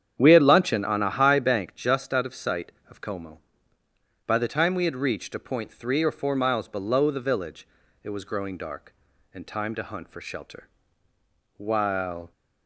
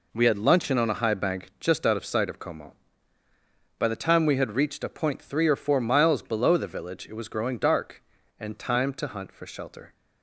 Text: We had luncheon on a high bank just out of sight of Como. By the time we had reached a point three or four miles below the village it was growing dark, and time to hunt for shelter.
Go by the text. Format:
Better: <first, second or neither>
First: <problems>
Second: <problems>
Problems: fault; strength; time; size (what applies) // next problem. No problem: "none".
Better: second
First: starts louder than the rest; strong; until 1.2 s; 8.5 dB // pauses between "village" and "it"; slight; at 7.6 s; 0.36 s long // goes on to say "While"; noticeable; from 11.5 s on; 0.74 s long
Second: none